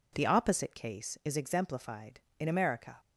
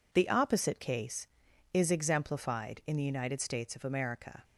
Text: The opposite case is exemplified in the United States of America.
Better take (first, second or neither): second